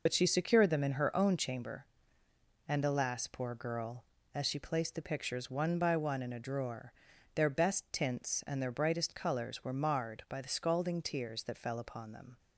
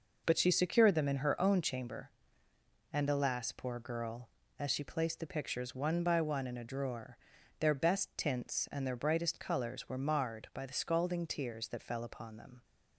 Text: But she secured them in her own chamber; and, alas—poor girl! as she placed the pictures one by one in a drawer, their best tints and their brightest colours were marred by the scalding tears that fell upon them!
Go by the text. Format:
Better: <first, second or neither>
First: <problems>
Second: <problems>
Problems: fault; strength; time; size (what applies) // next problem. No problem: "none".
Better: second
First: loses the start of "But"; at 0.0 s; 50 ms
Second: none